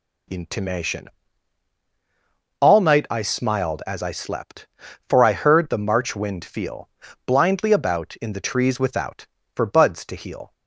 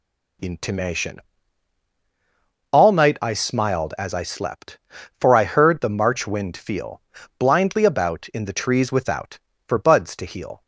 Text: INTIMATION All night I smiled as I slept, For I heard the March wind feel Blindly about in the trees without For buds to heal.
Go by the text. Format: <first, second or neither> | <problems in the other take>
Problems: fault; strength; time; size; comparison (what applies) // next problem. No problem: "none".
neither | pauses between "INTIMATION" and "All"; strong; the same in both // pauses between "feel" and "Blindly"; slight; the same in both